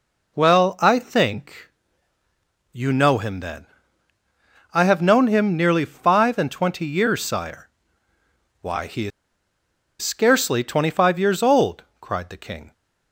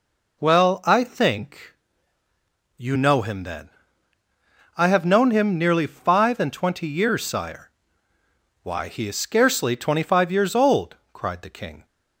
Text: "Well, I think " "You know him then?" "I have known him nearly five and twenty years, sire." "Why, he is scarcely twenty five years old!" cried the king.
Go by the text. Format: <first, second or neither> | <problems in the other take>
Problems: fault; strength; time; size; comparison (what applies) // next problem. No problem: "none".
second | pauses between "is" and "scarcely"; noticeable; at 9.1 s; 0.91 s long